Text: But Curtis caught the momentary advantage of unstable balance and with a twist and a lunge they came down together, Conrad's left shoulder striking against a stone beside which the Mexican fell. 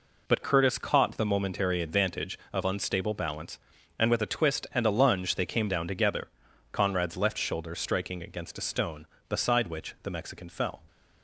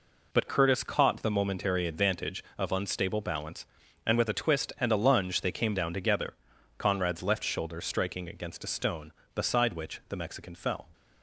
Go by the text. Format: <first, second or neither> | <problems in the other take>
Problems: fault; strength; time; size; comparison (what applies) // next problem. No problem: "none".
neither | none